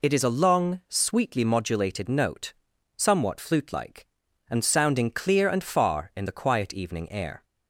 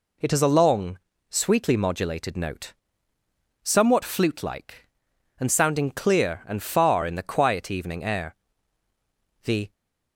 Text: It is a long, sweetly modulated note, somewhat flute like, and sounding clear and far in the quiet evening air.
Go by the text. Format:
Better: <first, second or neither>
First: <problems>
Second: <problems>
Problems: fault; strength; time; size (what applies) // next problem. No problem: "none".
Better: first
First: none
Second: goes on to say "The"; slight; from 9.4 s on; 0.30 s long